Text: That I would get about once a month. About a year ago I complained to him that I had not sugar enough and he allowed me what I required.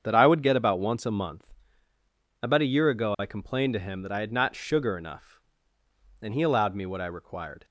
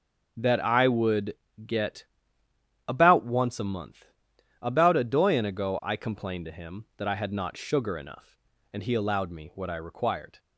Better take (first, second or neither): first